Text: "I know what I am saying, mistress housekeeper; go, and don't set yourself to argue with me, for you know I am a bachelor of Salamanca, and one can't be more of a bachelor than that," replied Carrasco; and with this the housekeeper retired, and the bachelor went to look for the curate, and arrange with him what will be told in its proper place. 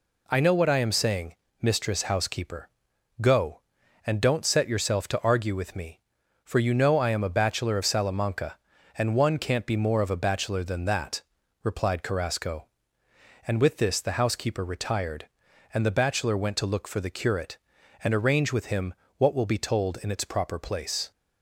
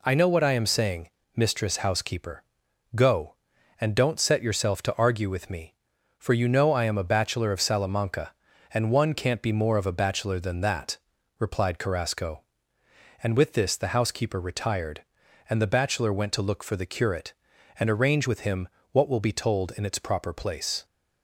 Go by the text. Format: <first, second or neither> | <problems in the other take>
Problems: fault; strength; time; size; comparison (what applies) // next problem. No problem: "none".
neither | pauses between "him" and "what"; slight; the same in both